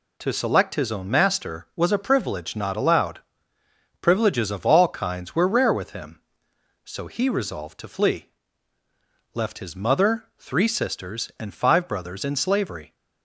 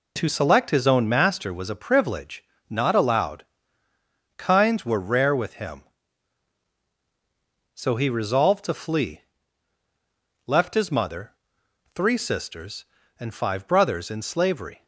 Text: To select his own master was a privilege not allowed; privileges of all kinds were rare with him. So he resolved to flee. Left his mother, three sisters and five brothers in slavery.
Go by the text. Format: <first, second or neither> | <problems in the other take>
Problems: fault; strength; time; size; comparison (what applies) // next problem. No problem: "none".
first | pauses between "privilege" and "not"; slight; at 2.4 s; 0.28 s long // skips "privileges of all"; at 3.9 s